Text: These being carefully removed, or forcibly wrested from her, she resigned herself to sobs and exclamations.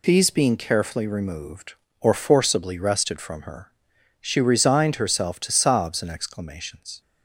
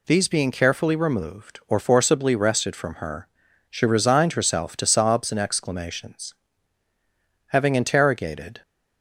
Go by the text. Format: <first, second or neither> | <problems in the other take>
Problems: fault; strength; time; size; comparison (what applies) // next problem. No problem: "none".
first | goes on to say "Having interrogated"; noticeable; from 7.4 s on; 1.1 s long